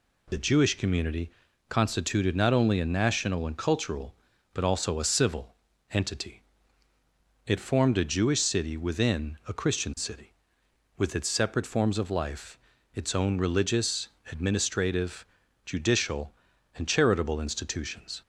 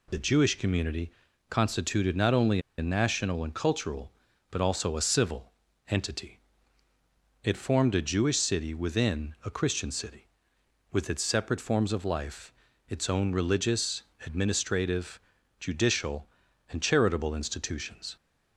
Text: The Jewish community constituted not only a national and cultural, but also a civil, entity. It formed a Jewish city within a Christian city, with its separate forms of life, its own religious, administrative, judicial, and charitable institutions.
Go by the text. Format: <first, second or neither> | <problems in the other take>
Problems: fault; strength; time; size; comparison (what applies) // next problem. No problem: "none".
first | pauses between "community" and "constituted"; at 1.1 s; 0.40 s long; also in the first // pauses between "only" and "a"; slight; at 2.5 s; 0.18 s long